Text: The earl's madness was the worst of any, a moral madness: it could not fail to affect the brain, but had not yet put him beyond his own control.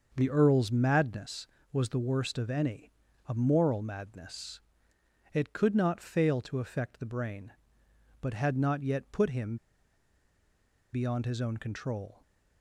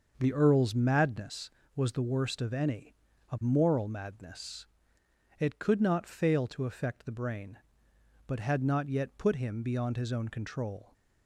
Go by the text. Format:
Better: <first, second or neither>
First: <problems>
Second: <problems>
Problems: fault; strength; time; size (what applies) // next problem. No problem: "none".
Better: second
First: starts louder than the rest; until 1.1 s; 6.5 dB // pauses between "him" and "beyond"; strong; at 9.5 s; 1.3 s long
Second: starts louder than the rest; until 1.1 s; 6.5 dB